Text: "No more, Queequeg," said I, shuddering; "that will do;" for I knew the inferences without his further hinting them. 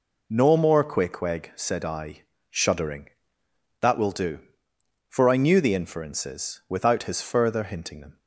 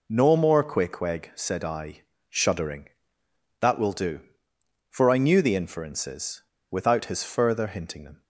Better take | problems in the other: first | pauses between "inferences" and "without"; slight; at 6.4 s; 0.28 s long

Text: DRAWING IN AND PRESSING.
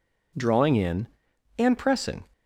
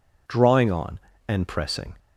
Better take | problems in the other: first | says "On" for "IN"; at 0.7 s

